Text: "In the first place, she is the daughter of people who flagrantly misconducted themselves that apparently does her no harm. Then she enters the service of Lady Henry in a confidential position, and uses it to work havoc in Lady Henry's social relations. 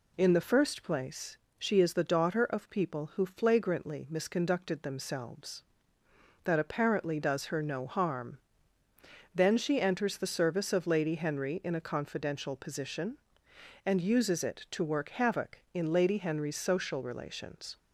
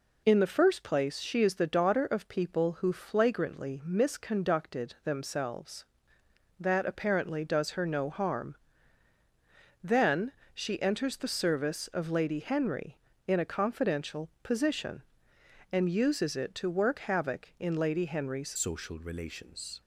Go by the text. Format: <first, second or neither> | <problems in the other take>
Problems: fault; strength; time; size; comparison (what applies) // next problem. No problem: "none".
first | pauses between "Then" and "she"; slight; at 10.3 s; 0.22 s long // changes voice at "social"; from 18.5 s on; 1.3 s long